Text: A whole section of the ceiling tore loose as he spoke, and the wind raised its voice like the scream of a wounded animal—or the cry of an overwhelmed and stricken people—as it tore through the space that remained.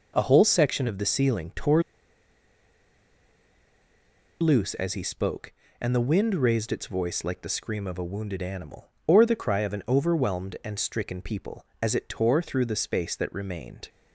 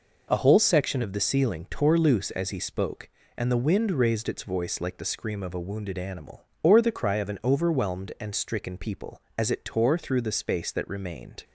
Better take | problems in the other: second | pauses between "tore" and "loose"; strong; at 1.8 s; 2.5 s long

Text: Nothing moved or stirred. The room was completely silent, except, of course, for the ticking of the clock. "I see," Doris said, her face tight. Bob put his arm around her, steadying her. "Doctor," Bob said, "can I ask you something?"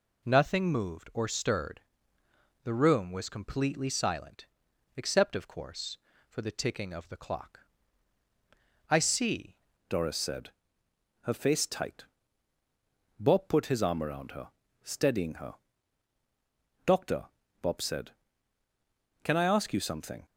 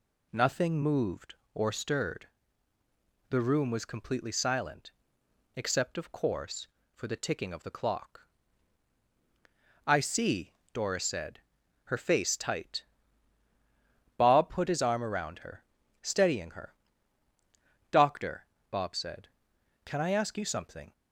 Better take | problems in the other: second | changes voice at "Doris"; from 9.8 s on; 10.4 s long

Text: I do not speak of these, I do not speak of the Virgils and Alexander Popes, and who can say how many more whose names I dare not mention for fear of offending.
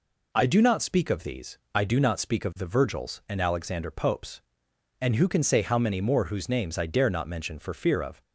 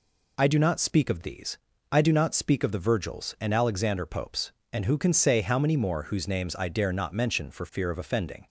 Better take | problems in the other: second | stops before "offending"; at 8.2 s

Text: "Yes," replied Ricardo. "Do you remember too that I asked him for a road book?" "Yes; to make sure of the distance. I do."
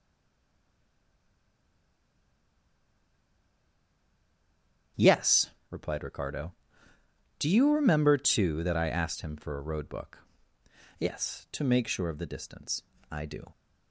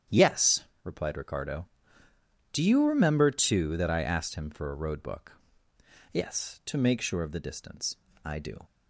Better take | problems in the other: second | stays silent before the first word; strong; until 4.9 s; 4.9 s long // starts louder than the rest; strong; until 6.1 s; 8.5 dB; strong in the second

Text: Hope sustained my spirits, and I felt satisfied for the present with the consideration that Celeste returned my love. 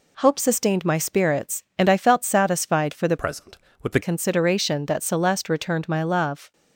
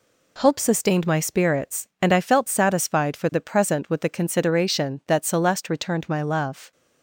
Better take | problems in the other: second | changes voice from "present" to "the"; from 3.1 to 4.0 s; 0.9 s long

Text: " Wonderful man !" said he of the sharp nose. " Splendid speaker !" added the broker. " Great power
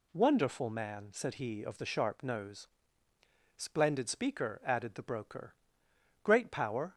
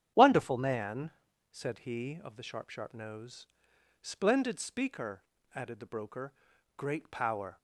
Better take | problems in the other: first | starts louder than the rest; strong; until 1.3 s; 10 dB // says "sharp" twice; at 2.6 s

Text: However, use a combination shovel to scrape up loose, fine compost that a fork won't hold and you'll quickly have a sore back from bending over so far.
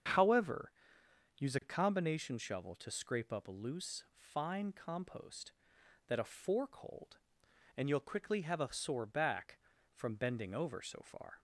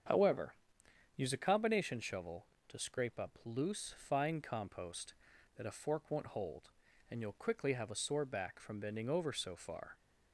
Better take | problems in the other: second | starts louder than the rest; strong; until 1.7 s; 7.5 dB; strong in the second // skips "won't"; at 6.7 s

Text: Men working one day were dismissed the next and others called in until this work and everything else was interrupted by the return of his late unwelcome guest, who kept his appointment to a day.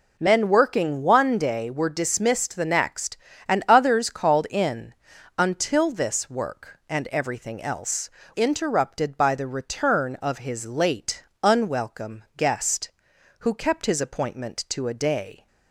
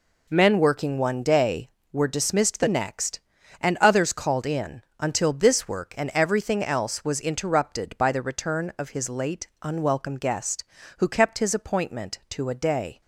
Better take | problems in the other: second | pauses between "in" and "until"; noticeable; at 4.9 s; 0.46 s long; slight in the second // skips "was"; at 8.2 s // pauses between "late" and "unwelcome"; slight; at 11.2 s; 0.20 s long; slight in the second

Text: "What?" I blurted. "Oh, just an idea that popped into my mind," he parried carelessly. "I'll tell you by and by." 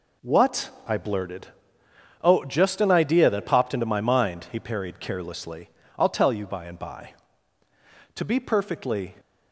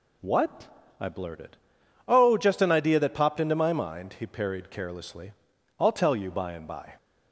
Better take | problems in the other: second | goes on to say "To be perfectly"; noticeable; from 8.1 s on; 1.0 s long

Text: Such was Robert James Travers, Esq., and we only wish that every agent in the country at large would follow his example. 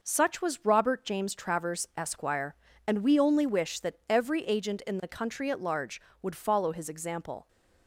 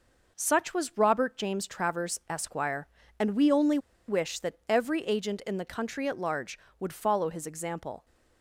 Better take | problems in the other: first | pauses between "only" and "wish"; slight; at 3.7 s; 0.30 s long

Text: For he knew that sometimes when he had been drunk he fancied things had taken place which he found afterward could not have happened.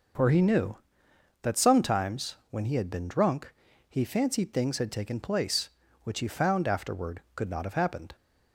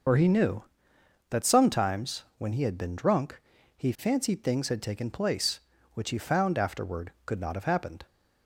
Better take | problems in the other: first | loses the start of "For"; at 0.0 s; 50 ms // pauses between "drunk" and "he"; slight; at 3.4 s; 0.36 s long; slight in the first

